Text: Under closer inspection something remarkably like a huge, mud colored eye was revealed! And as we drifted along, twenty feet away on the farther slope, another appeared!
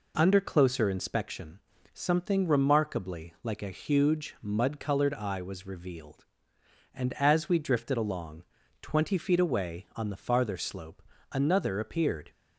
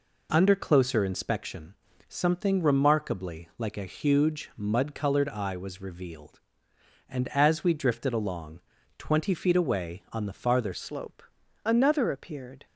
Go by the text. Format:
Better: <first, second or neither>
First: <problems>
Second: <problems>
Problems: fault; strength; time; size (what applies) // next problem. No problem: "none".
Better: first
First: pauses between "inspection" and "something"; slight; at 1.5 s; 0.32 s long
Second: pauses between "inspection" and "something"; slight; at 1.7 s; 0.32 s long // changes voice at "slope"; from 10.7 s on; 1.9 s long